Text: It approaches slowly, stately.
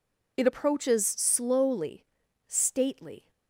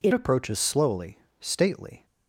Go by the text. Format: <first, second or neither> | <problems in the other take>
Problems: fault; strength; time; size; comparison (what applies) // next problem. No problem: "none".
first | changes voice at "approaches"; from 0.1 s on; 1.9 s long